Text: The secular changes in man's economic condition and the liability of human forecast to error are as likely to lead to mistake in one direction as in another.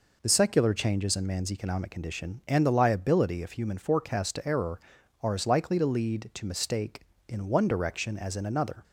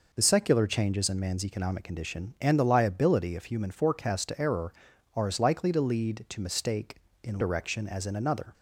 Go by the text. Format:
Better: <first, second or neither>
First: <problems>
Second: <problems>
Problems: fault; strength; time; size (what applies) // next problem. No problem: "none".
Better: first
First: none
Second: skips "one"; at 7.4 s